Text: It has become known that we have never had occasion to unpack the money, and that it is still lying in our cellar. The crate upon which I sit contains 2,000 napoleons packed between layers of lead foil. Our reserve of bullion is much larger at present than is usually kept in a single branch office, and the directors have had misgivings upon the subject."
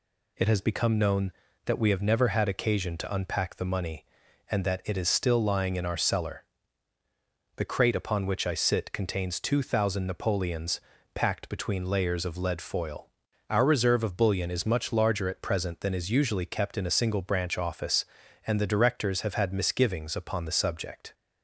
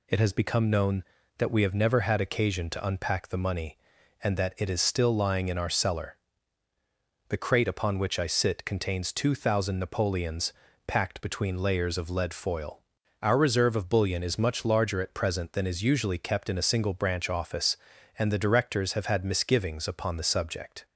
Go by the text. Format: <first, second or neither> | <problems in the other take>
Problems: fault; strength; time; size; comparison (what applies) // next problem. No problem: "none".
neither | pauses between "napoleons" and "packed"; slight; the same in both